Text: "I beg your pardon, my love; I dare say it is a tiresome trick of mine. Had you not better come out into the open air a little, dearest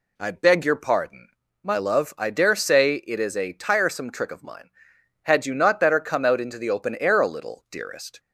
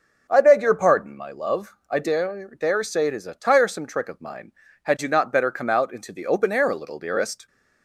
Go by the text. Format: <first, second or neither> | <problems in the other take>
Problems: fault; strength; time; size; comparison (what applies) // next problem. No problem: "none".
first | says "dare" twice; at 2.5 s